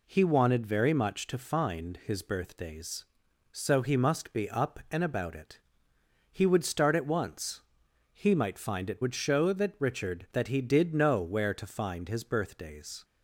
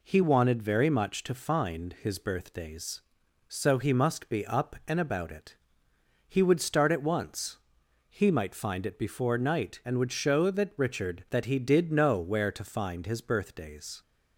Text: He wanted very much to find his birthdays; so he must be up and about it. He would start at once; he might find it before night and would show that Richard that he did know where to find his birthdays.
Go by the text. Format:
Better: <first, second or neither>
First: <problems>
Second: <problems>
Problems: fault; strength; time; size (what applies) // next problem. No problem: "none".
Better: second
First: skips "before night and"; at 9.0 s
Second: none